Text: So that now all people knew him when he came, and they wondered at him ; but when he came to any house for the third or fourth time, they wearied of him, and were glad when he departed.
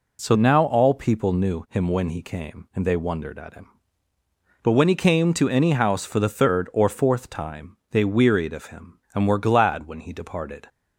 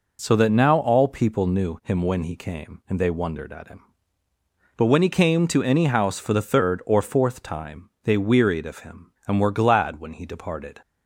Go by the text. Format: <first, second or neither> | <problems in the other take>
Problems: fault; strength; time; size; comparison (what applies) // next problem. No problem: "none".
second | skips "that"; at 0.3 s